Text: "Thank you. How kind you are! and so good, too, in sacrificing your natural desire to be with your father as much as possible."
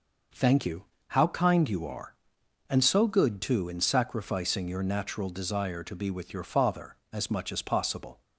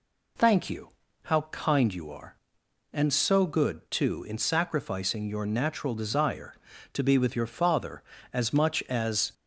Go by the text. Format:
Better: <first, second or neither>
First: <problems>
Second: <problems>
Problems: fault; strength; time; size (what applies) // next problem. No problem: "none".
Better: first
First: none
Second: stops before "possible"; at 9.3 s